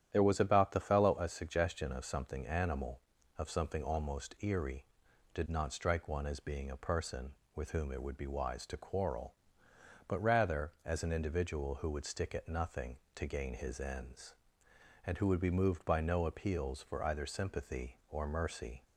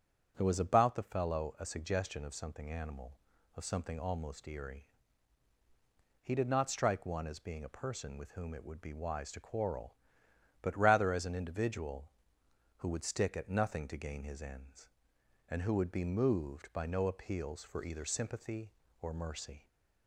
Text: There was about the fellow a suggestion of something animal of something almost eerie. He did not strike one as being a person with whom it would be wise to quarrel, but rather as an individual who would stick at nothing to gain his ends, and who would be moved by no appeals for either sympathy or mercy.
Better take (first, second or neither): second